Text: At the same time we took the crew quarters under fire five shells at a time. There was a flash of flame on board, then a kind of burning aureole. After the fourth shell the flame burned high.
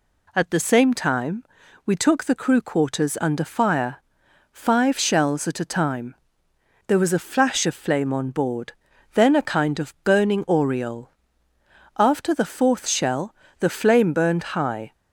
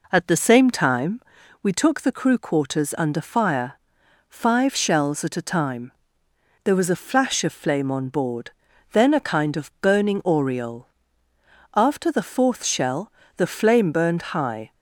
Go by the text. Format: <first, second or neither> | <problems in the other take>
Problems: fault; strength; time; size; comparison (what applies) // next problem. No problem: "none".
first | starts louder than the rest; noticeable; until 1.5 s; 4 dB // pauses between "time" and "we"; at 1.1 s; 0.44 s long; also in the first // pauses between "fire" and "five"; noticeable; at 3.7 s; 0.50 s long; noticeable in the first // pauses between "shell" and "the"; slight; at 13.1 s; 0.24 s long; slight in the first